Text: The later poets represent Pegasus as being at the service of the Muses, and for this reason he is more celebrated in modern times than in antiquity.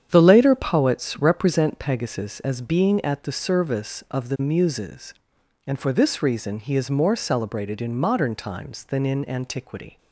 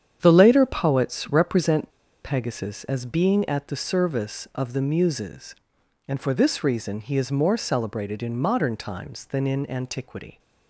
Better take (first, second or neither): first